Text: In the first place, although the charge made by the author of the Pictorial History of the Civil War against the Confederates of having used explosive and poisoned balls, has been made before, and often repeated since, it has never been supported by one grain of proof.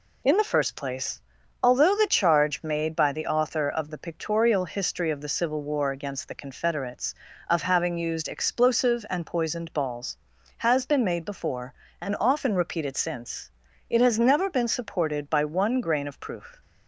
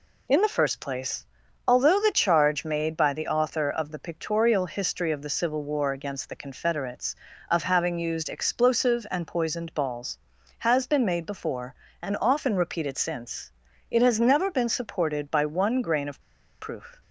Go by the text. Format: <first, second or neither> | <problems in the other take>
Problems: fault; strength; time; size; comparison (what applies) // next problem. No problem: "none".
first | pauses between "of" and "proof"; at 16.1 s; 0.41 s long